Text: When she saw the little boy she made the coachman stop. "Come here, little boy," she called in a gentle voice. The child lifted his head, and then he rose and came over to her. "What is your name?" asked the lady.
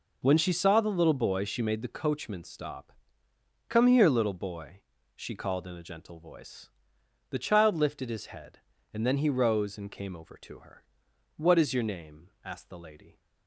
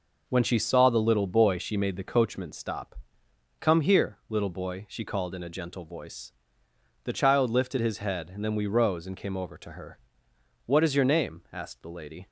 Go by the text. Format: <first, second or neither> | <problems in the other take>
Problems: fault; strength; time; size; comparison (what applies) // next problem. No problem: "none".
first | says "we" for "he"; at 8.5 s